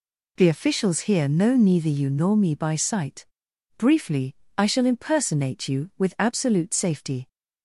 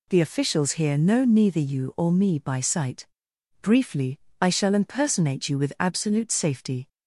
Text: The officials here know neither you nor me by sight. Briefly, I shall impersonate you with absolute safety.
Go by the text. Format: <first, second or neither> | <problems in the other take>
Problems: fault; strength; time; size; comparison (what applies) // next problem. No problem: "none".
first | says "or" for "nor"; at 1.9 s